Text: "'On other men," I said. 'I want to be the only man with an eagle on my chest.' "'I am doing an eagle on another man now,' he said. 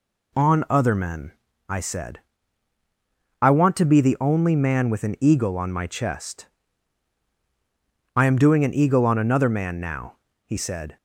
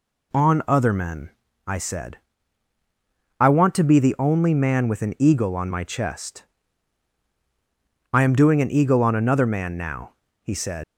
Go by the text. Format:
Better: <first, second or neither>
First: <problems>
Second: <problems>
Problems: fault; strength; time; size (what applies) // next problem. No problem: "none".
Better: first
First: none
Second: leaves "said" unfinished; at 10.8 s; 105 ms